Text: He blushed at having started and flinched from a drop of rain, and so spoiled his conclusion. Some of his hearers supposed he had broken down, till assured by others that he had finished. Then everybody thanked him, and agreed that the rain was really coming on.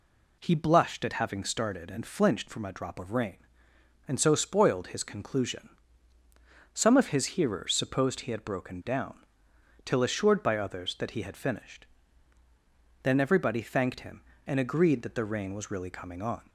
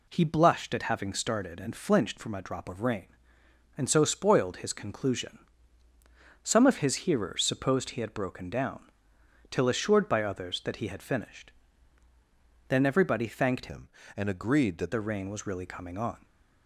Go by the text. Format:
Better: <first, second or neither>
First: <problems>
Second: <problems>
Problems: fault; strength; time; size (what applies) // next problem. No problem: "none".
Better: first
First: none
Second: changes voice from "him" to "that"; from 13.6 to 14.9 s; 1.3 s long